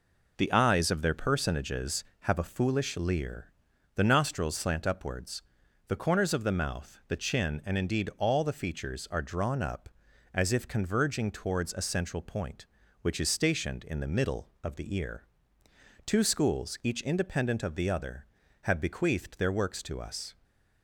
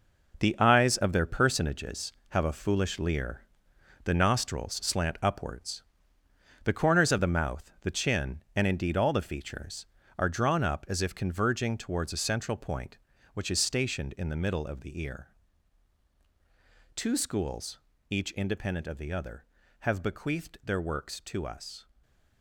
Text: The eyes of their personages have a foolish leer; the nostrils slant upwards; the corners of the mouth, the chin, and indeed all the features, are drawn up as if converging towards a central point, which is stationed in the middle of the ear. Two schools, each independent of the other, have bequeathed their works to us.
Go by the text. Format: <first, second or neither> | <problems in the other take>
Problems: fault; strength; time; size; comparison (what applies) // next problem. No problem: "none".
first | gets quieter; strong; throughout; 8.5 dB // stays silent after the last word; slight; from 21.8 s on; 0.6 s long; slight in the first